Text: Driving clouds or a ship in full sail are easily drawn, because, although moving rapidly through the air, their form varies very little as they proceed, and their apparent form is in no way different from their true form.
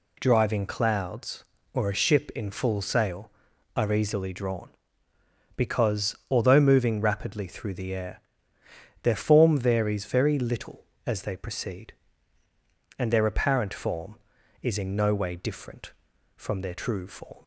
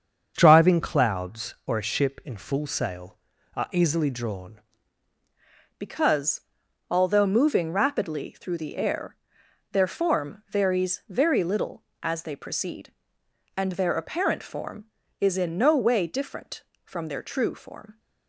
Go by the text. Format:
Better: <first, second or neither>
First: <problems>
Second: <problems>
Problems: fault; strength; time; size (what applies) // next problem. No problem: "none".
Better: first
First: none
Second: starts louder than the rest; until 1.3 s; 6.5 dB // changes voice at "because"; from 5.7 s on; 12.2 s long